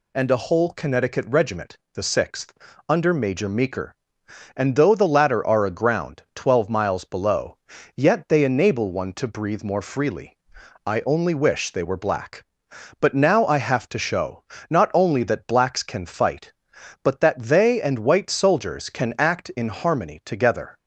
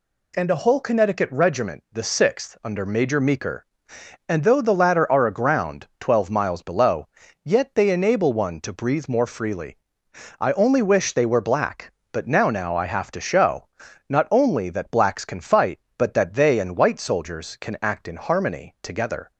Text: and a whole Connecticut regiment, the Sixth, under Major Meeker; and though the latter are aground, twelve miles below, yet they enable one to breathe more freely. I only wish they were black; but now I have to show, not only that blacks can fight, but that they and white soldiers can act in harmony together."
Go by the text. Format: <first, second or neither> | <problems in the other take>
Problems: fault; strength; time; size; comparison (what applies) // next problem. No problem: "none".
first | says "now" twice; at 12.5 s